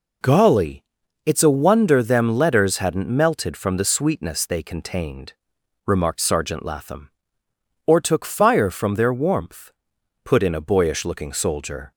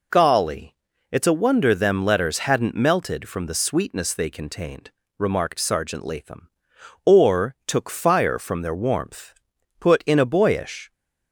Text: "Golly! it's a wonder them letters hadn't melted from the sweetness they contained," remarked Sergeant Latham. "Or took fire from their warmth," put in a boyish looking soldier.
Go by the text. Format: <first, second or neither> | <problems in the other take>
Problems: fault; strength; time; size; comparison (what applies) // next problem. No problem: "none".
first | stops before "looking soldier"; at 10.9 s